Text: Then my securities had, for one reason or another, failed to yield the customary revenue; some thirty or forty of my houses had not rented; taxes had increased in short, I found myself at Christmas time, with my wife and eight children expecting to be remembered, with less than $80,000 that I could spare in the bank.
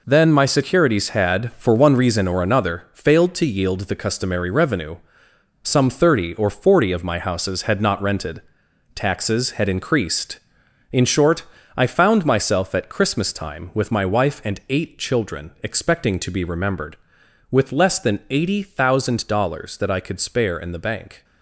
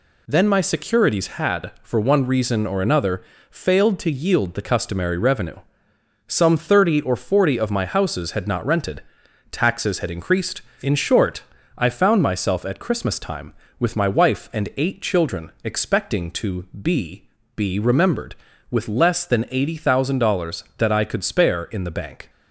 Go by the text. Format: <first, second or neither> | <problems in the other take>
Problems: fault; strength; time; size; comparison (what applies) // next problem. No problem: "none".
first | says "be" twice; at 17.5 s